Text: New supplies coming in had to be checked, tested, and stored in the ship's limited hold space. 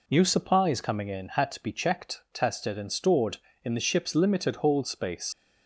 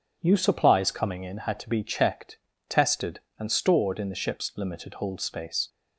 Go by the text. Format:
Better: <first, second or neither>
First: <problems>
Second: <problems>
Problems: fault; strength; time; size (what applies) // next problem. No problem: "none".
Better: second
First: leaves "space" unfinished; at 5.3 s; 75 ms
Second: none